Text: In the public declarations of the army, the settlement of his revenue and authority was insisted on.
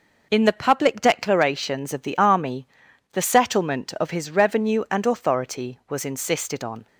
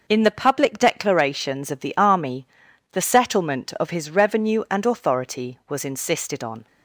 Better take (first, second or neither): neither